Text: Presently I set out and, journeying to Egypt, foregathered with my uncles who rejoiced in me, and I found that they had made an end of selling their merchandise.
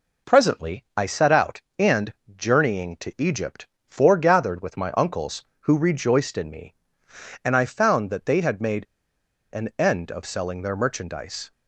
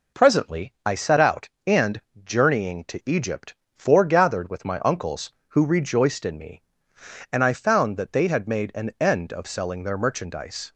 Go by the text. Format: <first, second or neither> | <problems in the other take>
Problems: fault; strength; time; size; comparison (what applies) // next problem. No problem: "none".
second | pauses between "made" and "an"; noticeable; at 8.8 s; 0.67 s long